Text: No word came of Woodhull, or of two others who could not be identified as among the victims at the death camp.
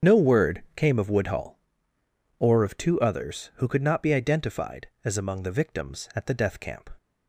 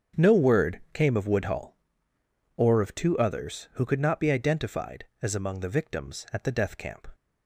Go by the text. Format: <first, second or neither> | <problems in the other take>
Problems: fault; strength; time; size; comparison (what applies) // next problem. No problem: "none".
second | loses the start of "No"; at 0.0 s; 70 ms // starts louder than the rest; until 1.1 s; 7 dB; also in the second